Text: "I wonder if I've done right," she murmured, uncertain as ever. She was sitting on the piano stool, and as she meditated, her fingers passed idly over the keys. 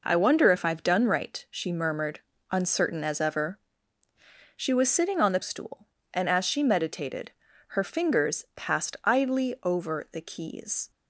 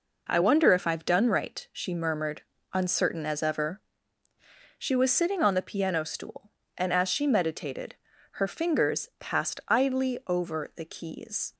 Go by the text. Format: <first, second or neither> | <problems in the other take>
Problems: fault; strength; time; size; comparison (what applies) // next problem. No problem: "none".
second | skips "piano"; at 5.4 s